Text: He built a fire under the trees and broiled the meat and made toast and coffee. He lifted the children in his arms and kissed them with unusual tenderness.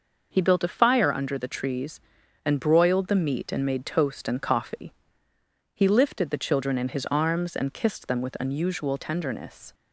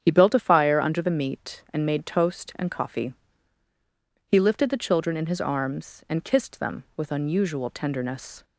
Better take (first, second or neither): first